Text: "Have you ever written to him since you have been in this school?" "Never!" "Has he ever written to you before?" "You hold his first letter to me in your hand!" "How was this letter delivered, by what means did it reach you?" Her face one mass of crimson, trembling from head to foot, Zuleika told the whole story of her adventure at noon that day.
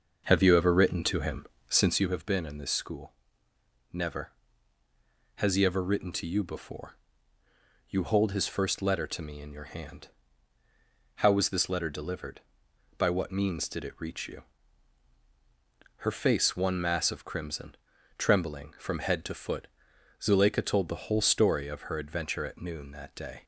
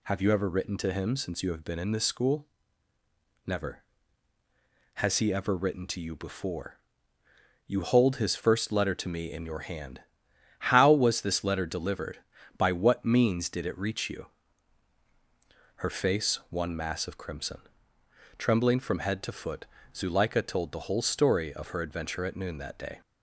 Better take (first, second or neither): second